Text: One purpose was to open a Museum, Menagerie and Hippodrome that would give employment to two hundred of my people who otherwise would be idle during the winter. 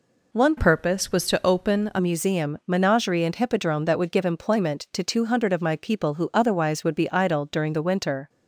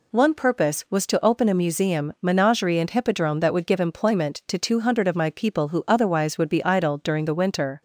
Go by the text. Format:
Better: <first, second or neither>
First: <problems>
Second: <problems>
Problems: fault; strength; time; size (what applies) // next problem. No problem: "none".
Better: second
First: changes voice from "purpose" to "a"; from 0.5 to 1.9 s; 1.4 s long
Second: none